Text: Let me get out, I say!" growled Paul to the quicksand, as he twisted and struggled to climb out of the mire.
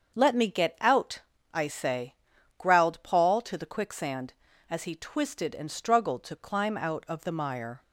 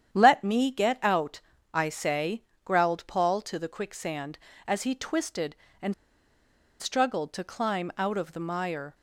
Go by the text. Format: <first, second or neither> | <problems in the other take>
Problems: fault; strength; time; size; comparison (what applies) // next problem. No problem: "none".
first | starts louder than the rest; strong; until 1.1 s; 9 dB; also in the first // pauses between "and" and "struggled"; noticeable; at 5.9 s; 0.86 s long